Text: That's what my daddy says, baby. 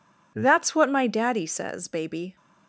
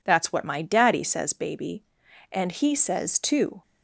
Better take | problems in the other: first | goes on to say "And he says too"; noticeable; from 2.3 s on; 1.2 s long

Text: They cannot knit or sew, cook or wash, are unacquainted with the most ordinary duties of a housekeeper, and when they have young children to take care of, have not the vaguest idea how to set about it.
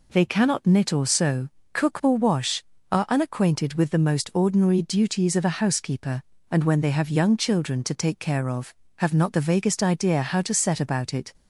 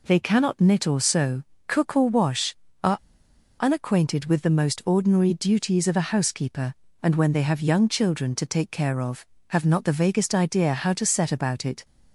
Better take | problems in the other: first | pauses between "are" and "unacquainted"; noticeable; at 2.9 s; 0.62 s long

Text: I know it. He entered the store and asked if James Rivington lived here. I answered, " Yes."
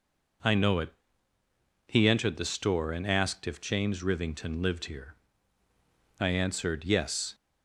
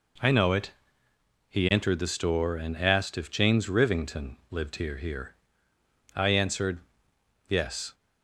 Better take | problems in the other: first | says "here" twice; at 4.9 s

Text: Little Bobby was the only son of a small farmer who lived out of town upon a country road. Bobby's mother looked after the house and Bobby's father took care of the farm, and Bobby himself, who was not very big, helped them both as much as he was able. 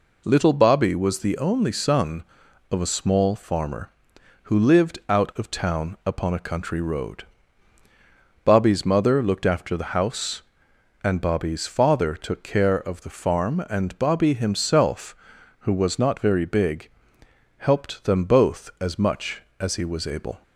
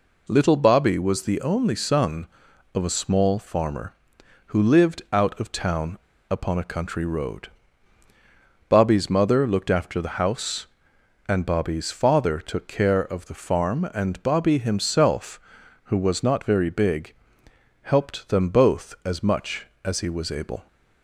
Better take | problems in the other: first | pauses between "town" and "upon"; slight; at 5.9 s; 0.33 s long

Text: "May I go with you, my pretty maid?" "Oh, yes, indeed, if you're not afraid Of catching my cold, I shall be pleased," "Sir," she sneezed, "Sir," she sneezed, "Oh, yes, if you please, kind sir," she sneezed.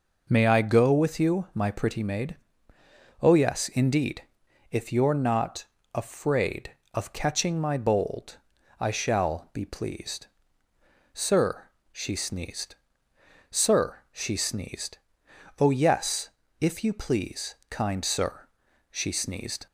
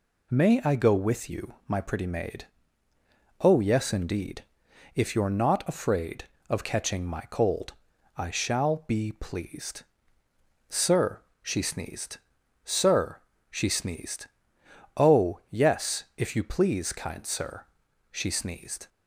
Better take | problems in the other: second | pauses between "not" and "afraid"; slight; at 5.6 s; 0.30 s long // says "bold" for "cold"; at 7.7 s

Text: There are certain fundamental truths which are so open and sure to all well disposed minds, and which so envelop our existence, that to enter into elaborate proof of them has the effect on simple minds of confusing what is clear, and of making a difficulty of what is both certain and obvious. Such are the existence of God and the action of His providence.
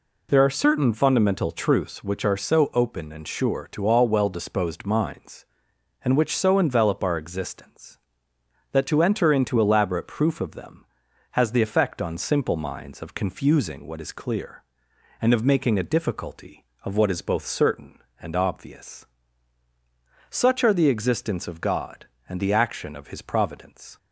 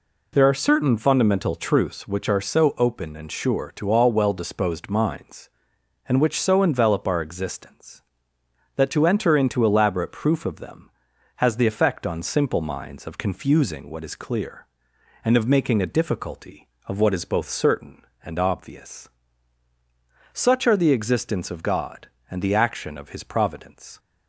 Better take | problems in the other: neither | none

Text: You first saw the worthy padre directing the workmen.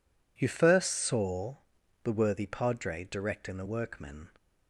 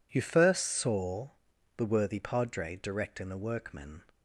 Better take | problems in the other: neither | pauses between "saw" and "the"; noticeable; the same in both

